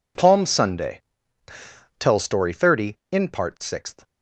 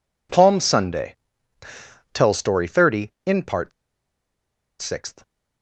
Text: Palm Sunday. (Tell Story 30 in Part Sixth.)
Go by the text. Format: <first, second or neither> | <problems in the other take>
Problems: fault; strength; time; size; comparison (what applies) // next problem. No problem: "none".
first | pauses between "Part" and "Sixth"; at 3.7 s; 1.1 s long